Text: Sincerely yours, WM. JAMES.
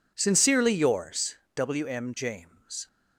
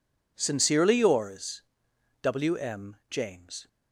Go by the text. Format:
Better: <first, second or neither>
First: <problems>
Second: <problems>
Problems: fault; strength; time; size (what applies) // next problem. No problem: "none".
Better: neither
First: none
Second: none